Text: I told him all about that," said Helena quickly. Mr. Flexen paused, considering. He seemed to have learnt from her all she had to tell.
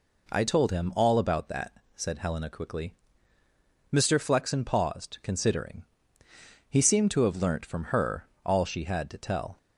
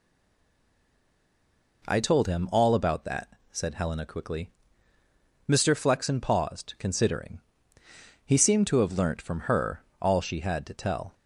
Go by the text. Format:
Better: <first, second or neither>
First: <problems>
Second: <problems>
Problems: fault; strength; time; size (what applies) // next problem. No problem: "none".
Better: first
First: pauses between "her" and "all"; slight; at 8.2 s; 0.18 s long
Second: stays silent before the first word; noticeable; until 1.8 s; 1.8 s long // pauses between "her" and "all"; slight; at 9.8 s; 0.18 s long